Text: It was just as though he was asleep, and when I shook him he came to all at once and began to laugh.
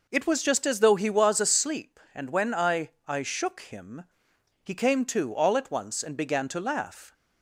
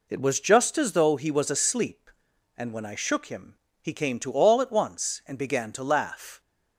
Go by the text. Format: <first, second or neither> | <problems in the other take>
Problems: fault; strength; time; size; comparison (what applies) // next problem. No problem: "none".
second | says "I" twice; at 3.0 s // pauses between "him" and "he"; noticeable; at 4.0 s; 0.60 s long; slight in the second